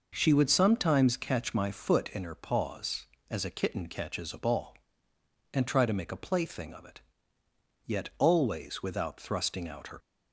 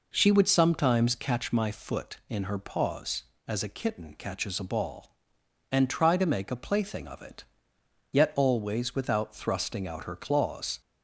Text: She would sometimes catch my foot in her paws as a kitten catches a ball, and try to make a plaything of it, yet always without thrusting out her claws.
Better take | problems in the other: second | stops before "claws"; at 9.9 s

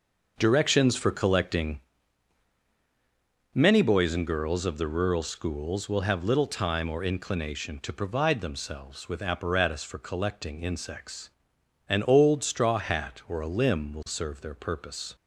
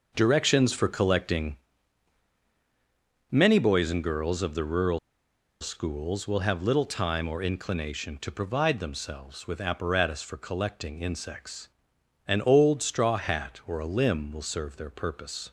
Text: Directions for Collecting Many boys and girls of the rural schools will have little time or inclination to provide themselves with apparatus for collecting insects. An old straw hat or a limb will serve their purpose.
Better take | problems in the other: first | pauses between "Collecting" and "Many"; strong; at 1.5 s; 1.7 s long; strong in the first // pauses between "rural" and "schools"; noticeable; at 4.9 s; 0.62 s long

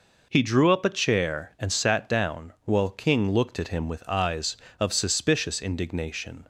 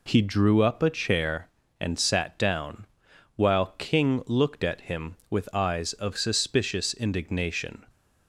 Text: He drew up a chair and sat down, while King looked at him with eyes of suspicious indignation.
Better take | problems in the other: neither | none

